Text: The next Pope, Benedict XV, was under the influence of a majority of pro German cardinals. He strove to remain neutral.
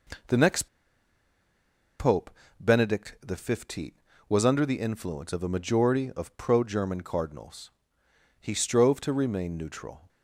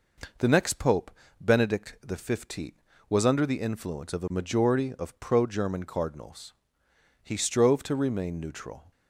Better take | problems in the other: second | pauses between "next" and "Pope"; strong; at 0.6 s; 1.3 s long

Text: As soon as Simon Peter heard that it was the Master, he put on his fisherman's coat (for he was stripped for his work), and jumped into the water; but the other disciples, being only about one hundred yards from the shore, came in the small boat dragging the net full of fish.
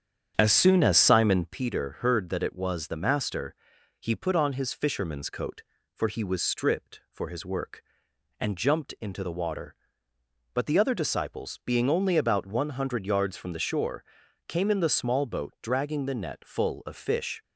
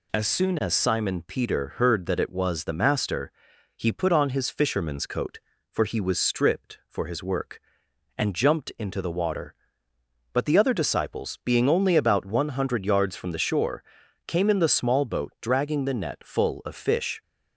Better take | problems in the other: second | starts louder than the rest; strong; until 1.6 s; 8.5 dB

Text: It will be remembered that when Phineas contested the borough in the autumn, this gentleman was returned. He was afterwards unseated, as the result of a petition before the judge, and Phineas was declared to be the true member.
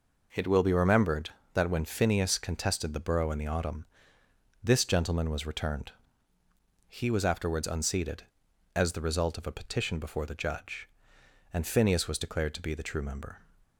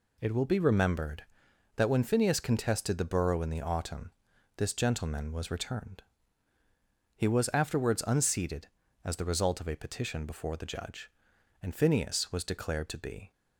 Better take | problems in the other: first | stops before "the true member"; at 13.3 s

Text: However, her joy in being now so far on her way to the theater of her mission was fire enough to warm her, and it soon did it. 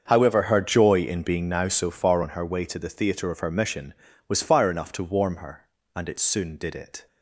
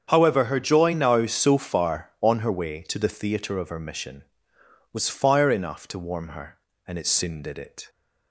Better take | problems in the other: first | starts louder than the rest; strong; until 1.1 s; 7.5 dB; also in the first // skips "in being"; at 0.9 s

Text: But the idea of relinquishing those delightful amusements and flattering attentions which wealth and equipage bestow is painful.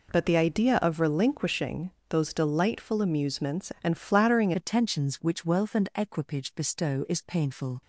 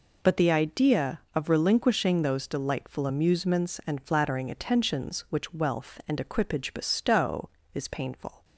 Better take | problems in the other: second | pauses between "relinquishing" and "those"; slight; at 1.9 s; 0.18 s long // changes voice at "attentions"; from 4.5 s on; 3.3 s long

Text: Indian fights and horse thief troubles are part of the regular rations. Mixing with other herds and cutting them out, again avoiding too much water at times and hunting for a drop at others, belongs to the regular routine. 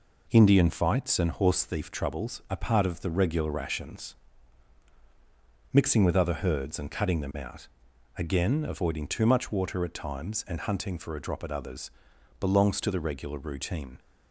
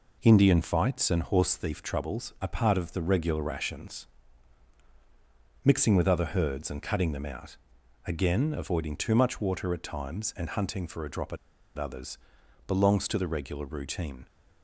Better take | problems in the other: first | pauses between "at" and "others"; at 11.3 s; 0.40 s long

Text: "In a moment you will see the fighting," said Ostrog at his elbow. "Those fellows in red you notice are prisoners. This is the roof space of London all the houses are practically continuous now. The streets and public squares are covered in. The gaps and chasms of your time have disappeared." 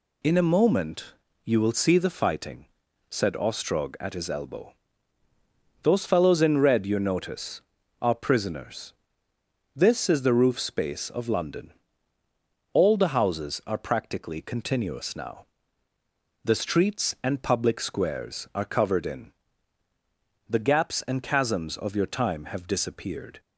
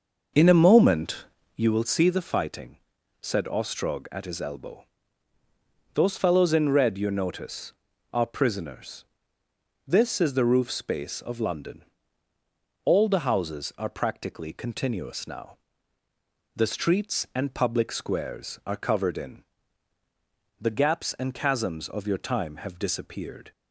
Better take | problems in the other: first | starts louder than the rest; noticeable; until 1.7 s; 6 dB // pauses between "moment" and "you"; slight; at 1.2 s; 0.30 s long; slight in the first // pauses between "London" and "all"; at 11.8 s; 1.0 s long; also in the first

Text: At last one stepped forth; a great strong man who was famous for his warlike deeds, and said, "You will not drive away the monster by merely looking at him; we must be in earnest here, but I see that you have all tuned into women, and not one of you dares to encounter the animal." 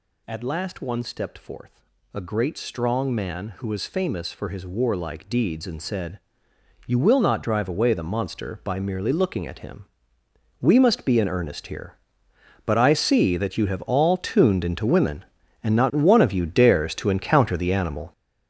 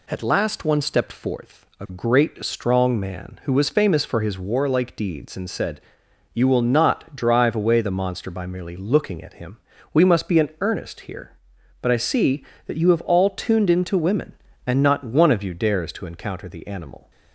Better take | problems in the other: second | gets louder; strong; throughout; 9 dB

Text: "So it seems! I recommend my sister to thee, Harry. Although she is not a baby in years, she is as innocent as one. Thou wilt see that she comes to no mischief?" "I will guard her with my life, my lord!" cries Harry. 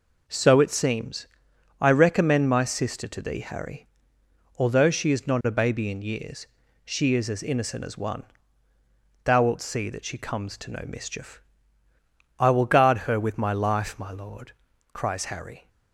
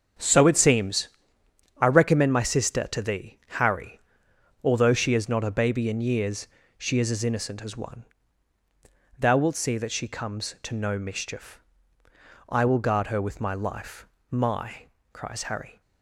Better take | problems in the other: first | starts louder than the rest; until 1.8 s; 7 dB // skips "lord"; at 14.9 s

